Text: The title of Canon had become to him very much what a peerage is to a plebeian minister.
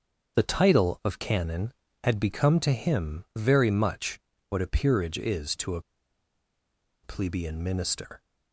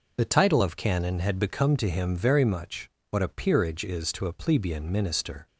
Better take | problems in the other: second | starts louder than the rest; until 1.4 s; 7 dB // pauses between "much" and "what"; slight; at 4.1 s; 0.30 s long; slight in the second // pauses between "a" and "plebeian"; at 5.8 s; 1.2 s long

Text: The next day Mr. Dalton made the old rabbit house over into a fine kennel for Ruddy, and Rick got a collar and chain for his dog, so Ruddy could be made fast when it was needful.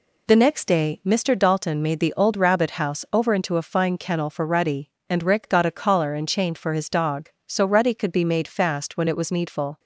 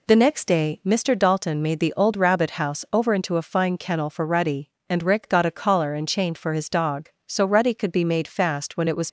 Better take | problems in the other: first | stops before "needful"; at 9.0 s

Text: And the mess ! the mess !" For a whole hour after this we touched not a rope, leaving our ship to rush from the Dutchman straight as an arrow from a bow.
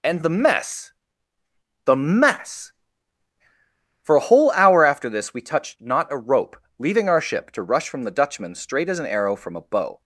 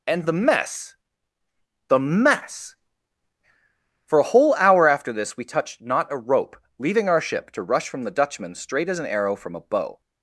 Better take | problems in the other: neither | none

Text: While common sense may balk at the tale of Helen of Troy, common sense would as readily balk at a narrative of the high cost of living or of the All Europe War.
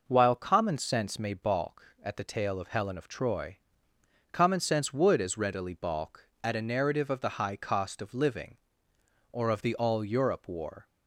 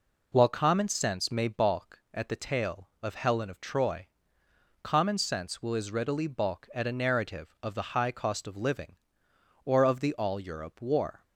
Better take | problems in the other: first | says "will" for "would"; at 5.6 s

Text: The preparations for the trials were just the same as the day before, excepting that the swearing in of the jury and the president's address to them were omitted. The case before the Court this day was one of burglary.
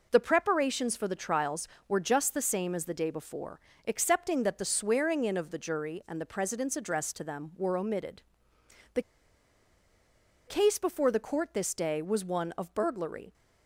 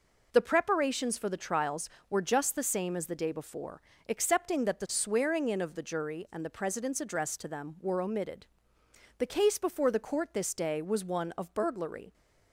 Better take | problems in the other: second | pauses between "The" and "case"; strong; at 9.0 s; 1.4 s long

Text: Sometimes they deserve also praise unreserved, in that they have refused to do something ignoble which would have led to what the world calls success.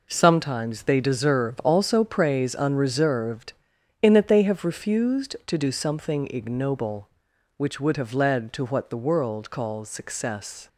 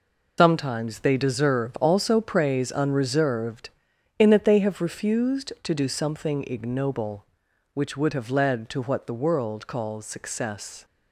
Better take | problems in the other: first | loses the start of "Sometimes"; at 0.3 s; 115 ms

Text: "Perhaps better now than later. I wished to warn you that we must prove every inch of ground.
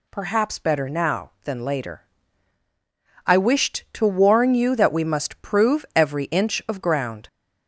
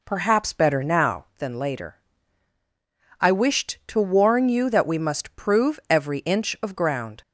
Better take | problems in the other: first | starts louder than the rest; until 1.4 s; 4 dB

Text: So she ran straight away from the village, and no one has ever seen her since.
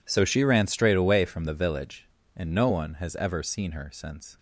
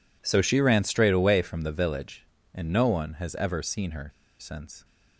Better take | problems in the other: first | pauses between "her" and "since"; slight; at 4.0 s; 0.30 s long

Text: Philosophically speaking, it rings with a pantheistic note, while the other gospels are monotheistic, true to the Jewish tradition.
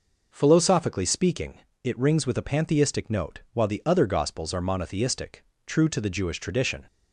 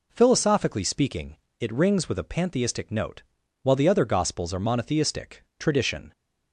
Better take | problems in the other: first | skips "true to the Jewish"; at 5.5 s

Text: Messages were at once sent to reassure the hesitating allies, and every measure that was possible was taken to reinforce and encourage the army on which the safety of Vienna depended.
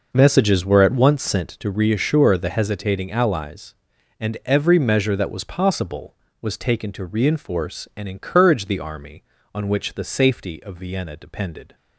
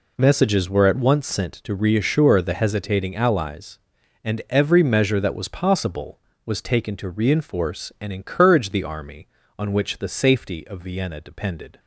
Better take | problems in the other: second | starts louder than the rest; noticeable; until 1.8 s; 5.5 dB

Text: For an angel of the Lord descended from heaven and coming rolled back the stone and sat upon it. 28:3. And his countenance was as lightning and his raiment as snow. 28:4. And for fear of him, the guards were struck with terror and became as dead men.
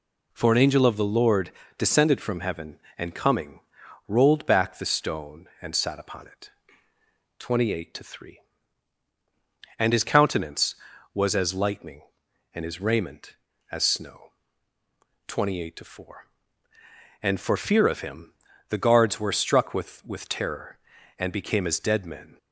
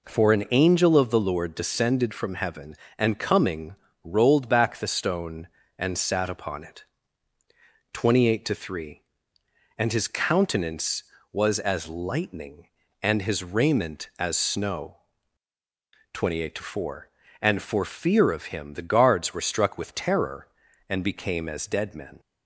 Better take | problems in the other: second | pauses between "Lord" and "descended"; slight; at 1.5 s; 0.26 s long // pauses between "coming" and "rolled"; noticeable; at 3.5 s; 0.48 s long; slight in the second // says "with" twice; at 20.0 s

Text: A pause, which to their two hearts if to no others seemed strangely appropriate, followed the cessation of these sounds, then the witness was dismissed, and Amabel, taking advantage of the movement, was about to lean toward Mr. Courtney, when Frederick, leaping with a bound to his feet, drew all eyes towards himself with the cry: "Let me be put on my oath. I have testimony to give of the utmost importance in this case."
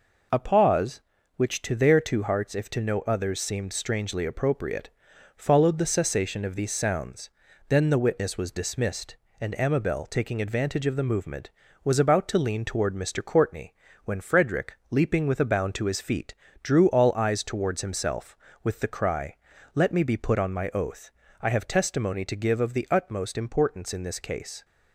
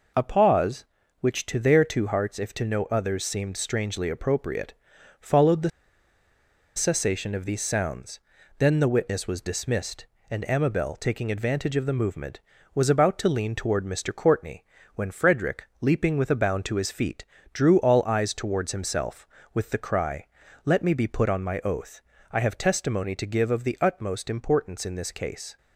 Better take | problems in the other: first | pauses between "the" and "cessation"; at 5.7 s; 1.0 s long

